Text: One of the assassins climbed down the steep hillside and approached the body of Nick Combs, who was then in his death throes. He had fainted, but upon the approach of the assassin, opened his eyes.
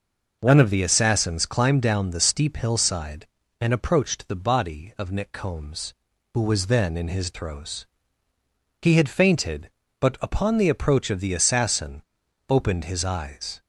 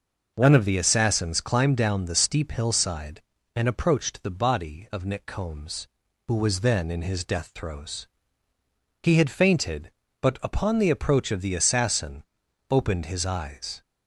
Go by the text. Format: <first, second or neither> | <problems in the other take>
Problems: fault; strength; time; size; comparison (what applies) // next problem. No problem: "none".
second | skips "death"; at 7.3 s